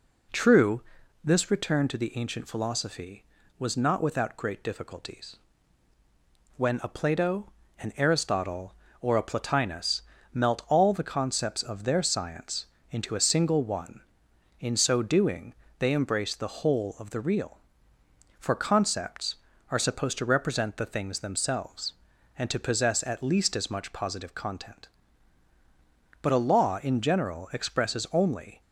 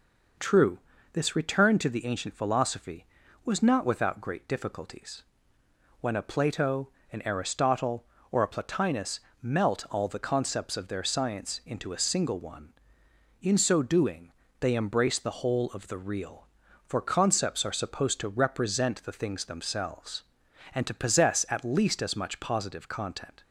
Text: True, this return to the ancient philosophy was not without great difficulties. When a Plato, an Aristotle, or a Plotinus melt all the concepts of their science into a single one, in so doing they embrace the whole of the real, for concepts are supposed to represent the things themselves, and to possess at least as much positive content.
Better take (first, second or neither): second